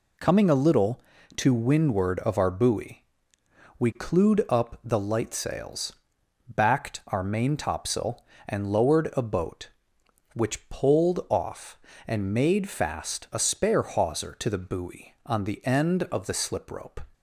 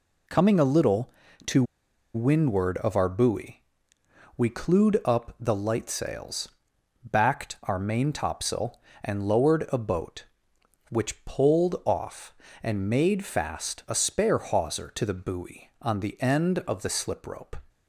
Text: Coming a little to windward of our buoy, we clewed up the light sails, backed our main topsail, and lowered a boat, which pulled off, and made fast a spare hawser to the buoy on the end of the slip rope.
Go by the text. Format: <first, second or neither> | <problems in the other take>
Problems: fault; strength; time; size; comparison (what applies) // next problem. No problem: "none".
first | pauses between "to" and "windward"; noticeable; at 1.6 s; 0.51 s long